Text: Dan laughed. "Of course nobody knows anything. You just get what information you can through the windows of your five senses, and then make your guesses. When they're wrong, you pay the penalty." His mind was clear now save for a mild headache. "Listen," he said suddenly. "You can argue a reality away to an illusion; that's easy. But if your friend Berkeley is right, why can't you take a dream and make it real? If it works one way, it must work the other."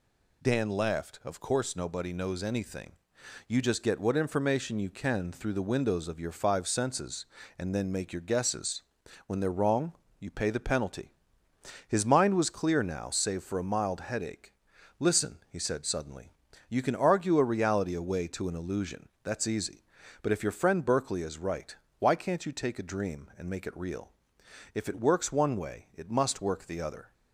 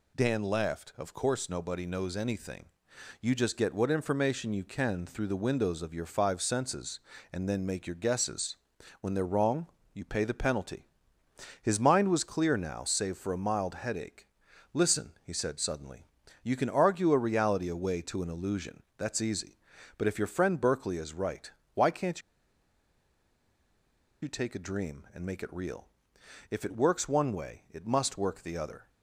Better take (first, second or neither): first